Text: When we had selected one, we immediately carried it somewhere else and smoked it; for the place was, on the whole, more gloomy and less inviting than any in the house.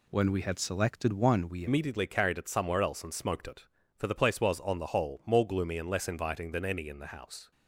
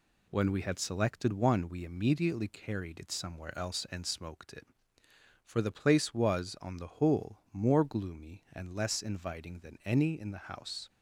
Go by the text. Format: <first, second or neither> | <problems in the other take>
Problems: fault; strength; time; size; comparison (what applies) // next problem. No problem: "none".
second | changes voice at "immediately"; from 1.6 s on; 5.9 s long